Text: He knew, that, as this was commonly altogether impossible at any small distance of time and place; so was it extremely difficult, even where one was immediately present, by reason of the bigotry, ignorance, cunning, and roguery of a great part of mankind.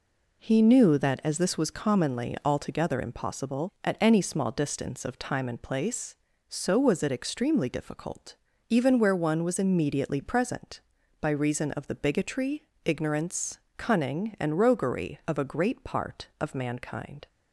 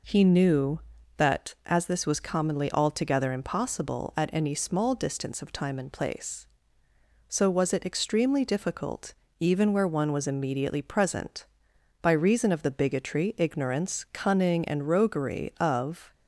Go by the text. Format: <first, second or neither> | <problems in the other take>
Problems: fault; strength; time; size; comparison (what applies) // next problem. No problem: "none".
first | stops before "a great part of mankind"; at 16.1 s